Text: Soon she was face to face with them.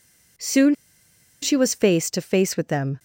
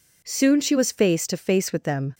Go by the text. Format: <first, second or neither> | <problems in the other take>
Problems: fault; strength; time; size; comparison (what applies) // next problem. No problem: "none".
second | pauses between "Soon" and "she"; noticeable; at 0.7 s; 0.67 s long